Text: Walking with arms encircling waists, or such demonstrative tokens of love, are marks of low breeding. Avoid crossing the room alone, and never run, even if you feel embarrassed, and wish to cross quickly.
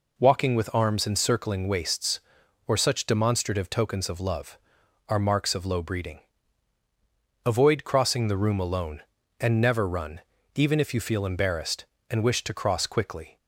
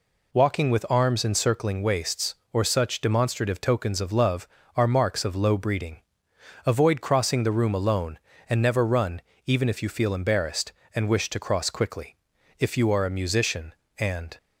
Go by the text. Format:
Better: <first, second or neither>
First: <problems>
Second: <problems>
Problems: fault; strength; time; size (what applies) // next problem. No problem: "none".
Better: first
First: none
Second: goes on to say "If you are a musician and"; strong; from 12.5 s on; 1.7 s long